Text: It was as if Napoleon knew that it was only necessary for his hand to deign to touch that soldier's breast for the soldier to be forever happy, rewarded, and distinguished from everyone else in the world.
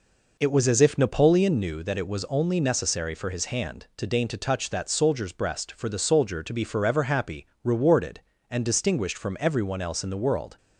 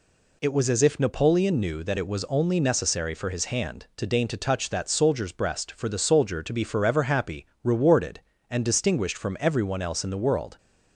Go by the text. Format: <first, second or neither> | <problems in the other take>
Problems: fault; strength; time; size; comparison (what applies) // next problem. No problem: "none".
second | starts louder than the rest; noticeable; until 1.6 s; 4.5 dB